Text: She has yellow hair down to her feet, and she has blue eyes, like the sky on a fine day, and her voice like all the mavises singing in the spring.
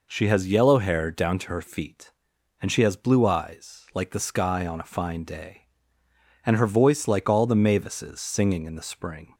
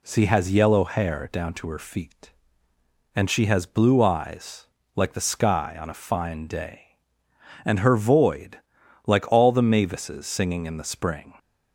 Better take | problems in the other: first | says "void" for "voice"; at 7.9 s

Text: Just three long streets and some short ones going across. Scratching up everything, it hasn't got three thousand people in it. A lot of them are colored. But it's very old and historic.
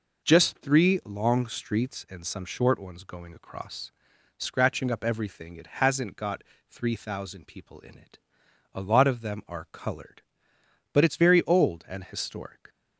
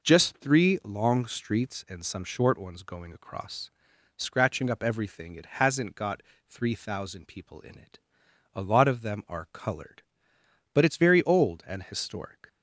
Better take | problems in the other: neither | pauses between "got" and "three"; slight; the same in both

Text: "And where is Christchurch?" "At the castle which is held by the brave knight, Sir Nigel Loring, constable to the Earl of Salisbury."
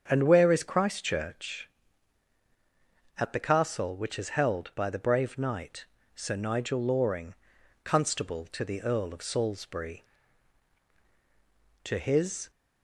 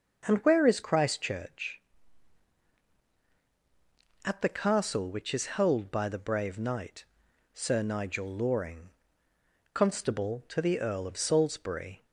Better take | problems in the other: second | starts louder than the rest; strong; until 1.1 s; 7 dB; also in the second // goes on to say "To his"; noticeable; from 11.8 s on; 0.68 s long

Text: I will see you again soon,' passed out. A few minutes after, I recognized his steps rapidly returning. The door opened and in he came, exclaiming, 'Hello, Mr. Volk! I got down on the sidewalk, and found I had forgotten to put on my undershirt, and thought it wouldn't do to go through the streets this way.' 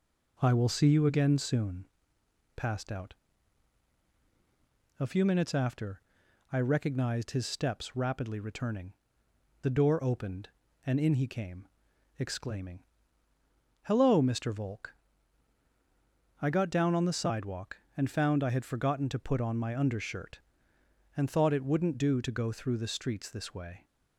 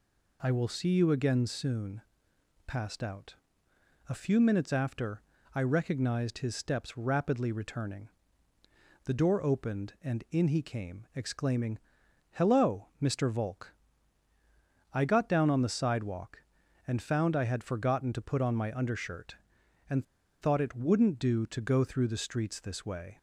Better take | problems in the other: first | pauses between "and" and "thought"; at 20.0 s; 0.38 s long

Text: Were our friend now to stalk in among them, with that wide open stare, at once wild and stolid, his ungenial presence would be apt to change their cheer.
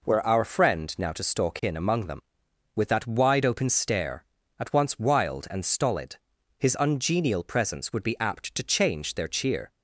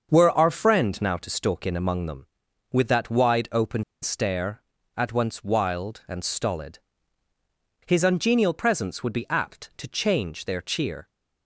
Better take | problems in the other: first | starts louder than the rest; until 1.1 s; 6.5 dB // pauses between "open" and "stare"; slight; at 3.8 s; 0.19 s long

